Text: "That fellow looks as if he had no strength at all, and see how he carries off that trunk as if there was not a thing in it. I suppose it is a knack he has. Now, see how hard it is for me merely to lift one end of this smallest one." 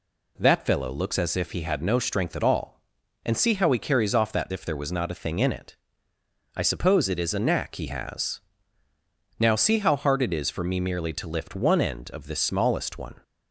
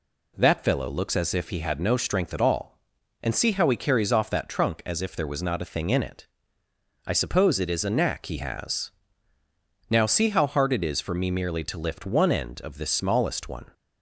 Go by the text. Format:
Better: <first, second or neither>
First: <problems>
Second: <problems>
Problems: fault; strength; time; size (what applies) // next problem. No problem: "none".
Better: second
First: skips "trunk as"; at 4.5 s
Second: none